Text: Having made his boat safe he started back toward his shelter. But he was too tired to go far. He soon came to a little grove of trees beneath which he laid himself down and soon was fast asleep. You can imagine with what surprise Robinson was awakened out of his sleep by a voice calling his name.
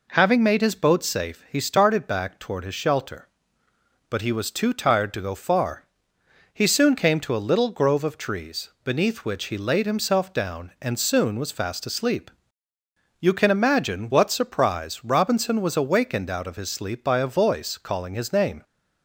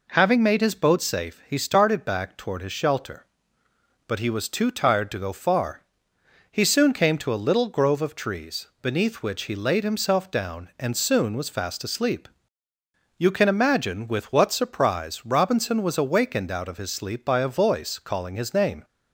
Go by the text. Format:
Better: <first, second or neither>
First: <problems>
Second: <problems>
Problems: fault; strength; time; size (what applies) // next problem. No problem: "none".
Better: second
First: skips "with"; at 14.0 s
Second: none